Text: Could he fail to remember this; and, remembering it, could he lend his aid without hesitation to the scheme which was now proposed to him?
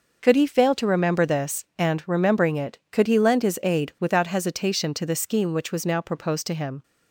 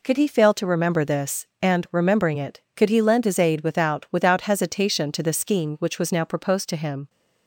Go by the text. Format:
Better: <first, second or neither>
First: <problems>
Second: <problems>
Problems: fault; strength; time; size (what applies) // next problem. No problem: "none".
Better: first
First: none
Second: says "without" twice; at 4.1 s